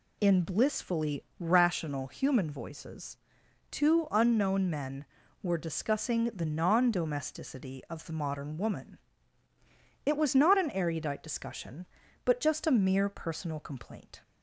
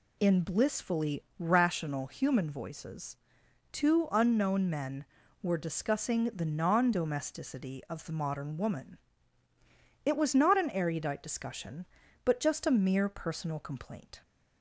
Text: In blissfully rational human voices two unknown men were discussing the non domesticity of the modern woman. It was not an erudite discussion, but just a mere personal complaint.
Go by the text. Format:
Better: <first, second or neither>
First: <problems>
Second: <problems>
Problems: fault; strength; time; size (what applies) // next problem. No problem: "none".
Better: neither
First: pauses between "blissfully" and "rational"; slight; at 1.2 s; 0.16 s long // pauses between "voices" and "two"; noticeable; at 3.1 s; 0.54 s long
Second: pauses between "blissfully" and "rational"; slight; at 1.2 s; 0.16 s long // pauses between "voices" and "two"; noticeable; at 3.1 s; 0.56 s long